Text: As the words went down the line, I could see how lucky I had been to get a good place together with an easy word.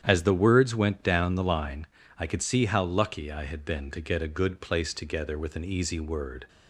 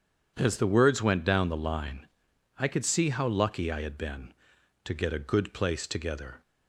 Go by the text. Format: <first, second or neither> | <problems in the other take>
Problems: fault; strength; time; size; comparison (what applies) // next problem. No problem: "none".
first | starts louder than the rest; strong; until 1.3 s; 8 dB; strong in the first // stops before "with an easy word"; at 6.4 s